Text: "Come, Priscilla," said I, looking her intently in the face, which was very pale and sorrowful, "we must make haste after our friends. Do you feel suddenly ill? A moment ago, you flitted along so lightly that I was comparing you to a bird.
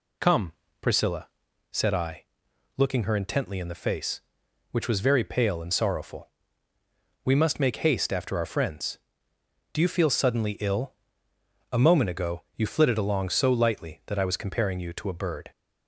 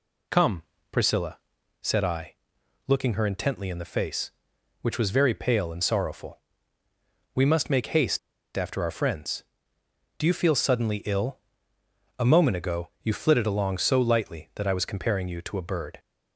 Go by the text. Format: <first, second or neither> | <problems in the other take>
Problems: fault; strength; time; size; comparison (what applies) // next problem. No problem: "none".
first | pauses between "haste" and "after"; at 8.1 s; 0.37 s long